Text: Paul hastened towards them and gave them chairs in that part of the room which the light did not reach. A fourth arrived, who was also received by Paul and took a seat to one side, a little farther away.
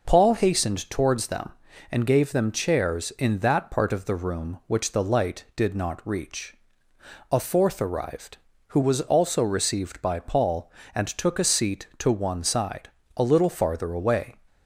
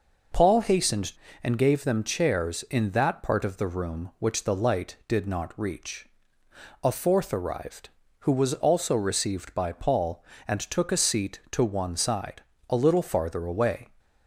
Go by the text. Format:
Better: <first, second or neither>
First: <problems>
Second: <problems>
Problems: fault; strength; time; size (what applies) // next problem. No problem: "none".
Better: first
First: none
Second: skips "towards them"; at 1.2 s